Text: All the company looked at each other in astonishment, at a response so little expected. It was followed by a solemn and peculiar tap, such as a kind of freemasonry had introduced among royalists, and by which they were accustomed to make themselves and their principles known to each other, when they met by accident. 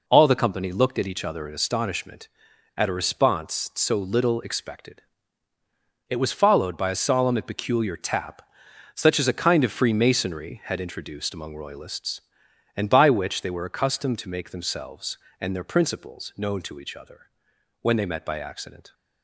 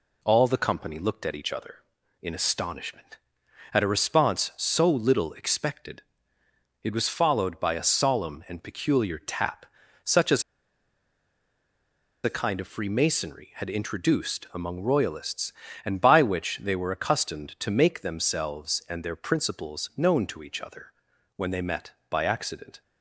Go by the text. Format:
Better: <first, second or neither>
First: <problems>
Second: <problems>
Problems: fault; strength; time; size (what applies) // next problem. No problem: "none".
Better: first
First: none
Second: pauses between "as" and "a"; strong; at 10.4 s; 1.8 s long